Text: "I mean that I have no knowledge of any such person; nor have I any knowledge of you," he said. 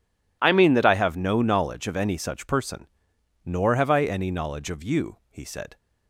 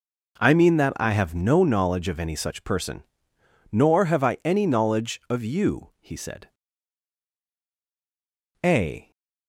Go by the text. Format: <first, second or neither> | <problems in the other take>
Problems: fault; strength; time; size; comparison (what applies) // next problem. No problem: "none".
first | goes on to say "A"; slight; from 8.6 s on; 0.48 s long